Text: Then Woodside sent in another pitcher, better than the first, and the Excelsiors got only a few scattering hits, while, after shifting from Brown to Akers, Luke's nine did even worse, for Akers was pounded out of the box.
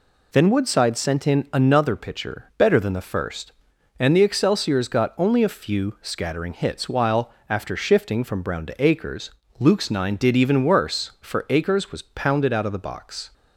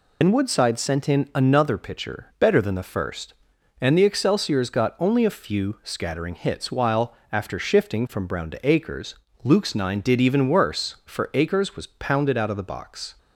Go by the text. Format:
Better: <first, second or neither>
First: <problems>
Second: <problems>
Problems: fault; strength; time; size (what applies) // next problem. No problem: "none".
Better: first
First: none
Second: loses the start of "Then"; at 0.2 s; 60 ms